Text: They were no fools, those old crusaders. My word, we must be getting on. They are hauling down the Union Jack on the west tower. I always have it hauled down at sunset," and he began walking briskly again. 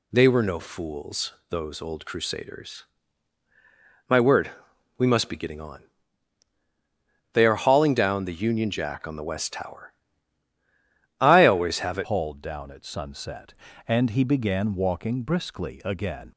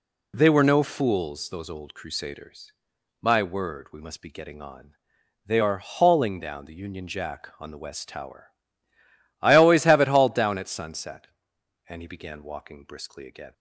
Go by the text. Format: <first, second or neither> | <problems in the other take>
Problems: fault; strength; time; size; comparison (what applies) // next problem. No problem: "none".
second | changes voice at "hauled"; from 12.0 s on; 4.3 s long